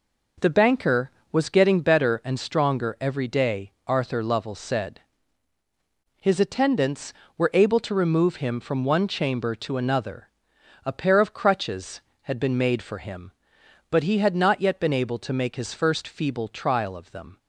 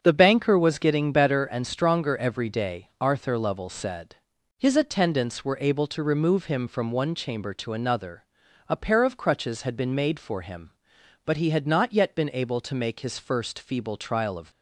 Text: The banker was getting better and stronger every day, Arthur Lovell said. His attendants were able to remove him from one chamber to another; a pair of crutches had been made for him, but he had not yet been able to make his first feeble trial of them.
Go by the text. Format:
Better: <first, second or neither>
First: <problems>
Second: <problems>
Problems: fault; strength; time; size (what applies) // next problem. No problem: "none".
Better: first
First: none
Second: starts louder than the rest; until 1.0 s; 7 dB // stops before "them"; at 14.5 s